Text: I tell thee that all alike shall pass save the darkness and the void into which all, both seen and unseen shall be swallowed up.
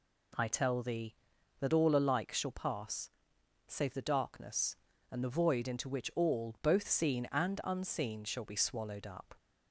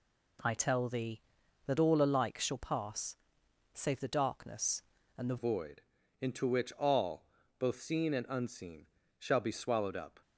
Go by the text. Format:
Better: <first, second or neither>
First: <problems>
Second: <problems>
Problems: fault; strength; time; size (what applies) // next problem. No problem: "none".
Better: first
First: pauses between "pass" and "save"; noticeable; at 3.0 s; 0.58 s long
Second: pauses between "pass" and "save"; noticeable; at 3.1 s; 0.58 s long // changes voice at "void"; from 5.3 s on; 4.9 s long // pauses between "void" and "into"; at 5.8 s; 0.40 s long // pauses between "unseen" and "shall"; slight; at 8.8 s; 0.30 s long